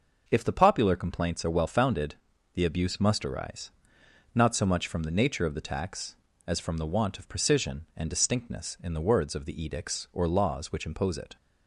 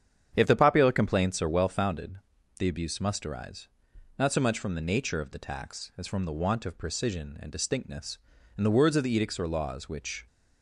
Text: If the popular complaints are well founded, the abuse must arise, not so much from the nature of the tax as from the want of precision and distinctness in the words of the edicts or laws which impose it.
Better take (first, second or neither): first